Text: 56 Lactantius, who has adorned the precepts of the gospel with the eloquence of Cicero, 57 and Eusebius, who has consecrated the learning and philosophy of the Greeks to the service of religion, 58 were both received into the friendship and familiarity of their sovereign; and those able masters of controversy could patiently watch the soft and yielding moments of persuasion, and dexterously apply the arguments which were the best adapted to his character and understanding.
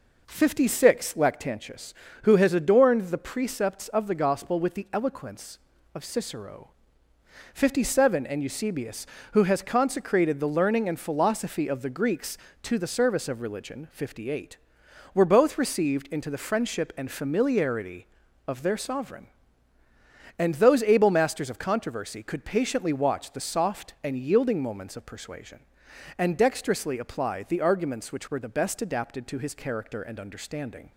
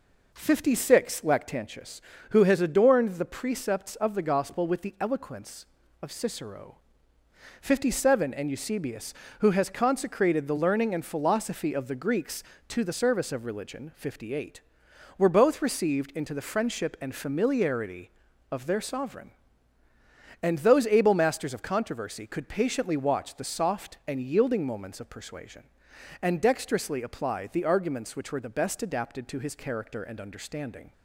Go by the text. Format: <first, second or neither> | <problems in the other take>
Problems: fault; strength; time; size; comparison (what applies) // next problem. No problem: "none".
neither | none